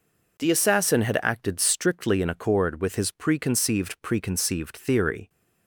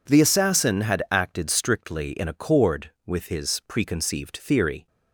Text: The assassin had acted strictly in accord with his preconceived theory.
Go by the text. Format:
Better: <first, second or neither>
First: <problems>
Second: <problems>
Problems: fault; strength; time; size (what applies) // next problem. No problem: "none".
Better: second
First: says "preconceived" twice; at 4.0 s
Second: none